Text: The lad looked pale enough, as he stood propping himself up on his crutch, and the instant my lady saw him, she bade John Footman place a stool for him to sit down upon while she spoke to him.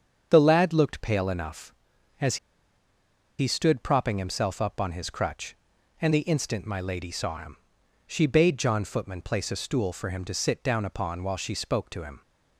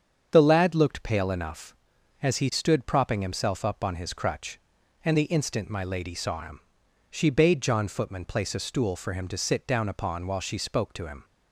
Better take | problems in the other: second | starts louder than the rest; strong; until 1.3 s; 7 dB; strong in the second // pauses between "as" and "he"; at 2.3 s; 1.0 s long

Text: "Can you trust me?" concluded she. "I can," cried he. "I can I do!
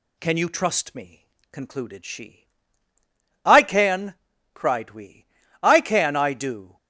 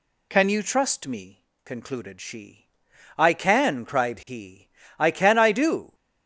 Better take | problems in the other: second | says "we" for "he"; at 4.9 s

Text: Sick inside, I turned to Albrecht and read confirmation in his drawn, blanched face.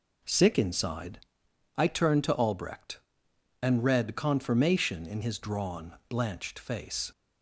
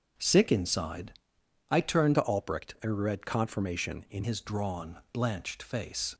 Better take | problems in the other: first | starts louder than the rest; strong; until 1.7 s; 7.5 dB // changes voice from "to" to "in"; from 2.1 to 4.2 s; 2.1 s long

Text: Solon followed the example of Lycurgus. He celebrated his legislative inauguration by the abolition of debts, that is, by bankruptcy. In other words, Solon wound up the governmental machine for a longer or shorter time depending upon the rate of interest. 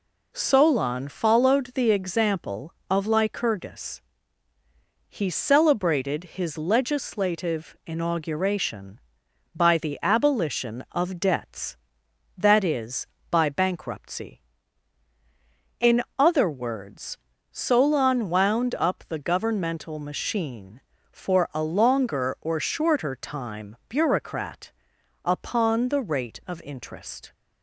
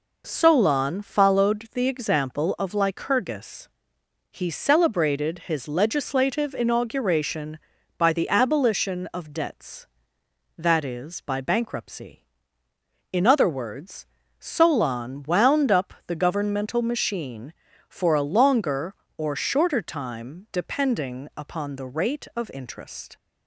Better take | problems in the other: second | pauses between "In" and "other"; slight; at 16.0 s; 0.16 s long // says "bureaucrat" for "depending"; at 23.8 s

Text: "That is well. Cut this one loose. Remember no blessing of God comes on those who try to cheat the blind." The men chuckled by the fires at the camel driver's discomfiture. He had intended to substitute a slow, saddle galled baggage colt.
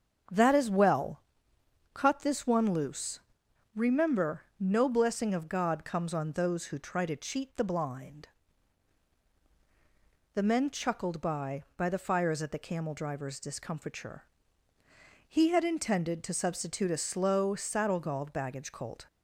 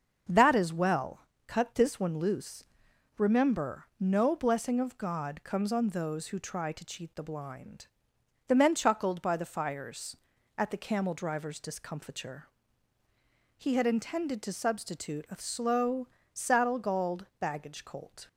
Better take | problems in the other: second | starts louder than the rest; until 2.0 s; 6.5 dB; also in the second // pauses between "Remember" and "no"; slight; at 4.4 s; 0.16 s long // says "by" twice; at 11.7 s

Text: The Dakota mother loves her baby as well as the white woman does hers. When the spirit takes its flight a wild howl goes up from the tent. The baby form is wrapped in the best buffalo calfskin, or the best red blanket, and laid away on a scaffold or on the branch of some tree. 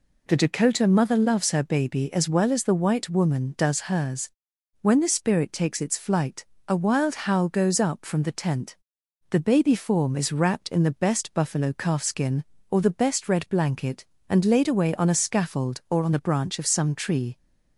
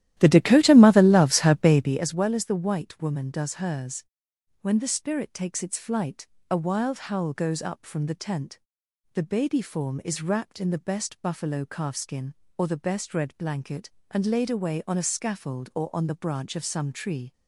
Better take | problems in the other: first | starts louder than the rest; strong; until 2.0 s; 13 dB // pauses between "flight" and "a"; slight; at 6.2 s; 0.22 s long; slight in the first

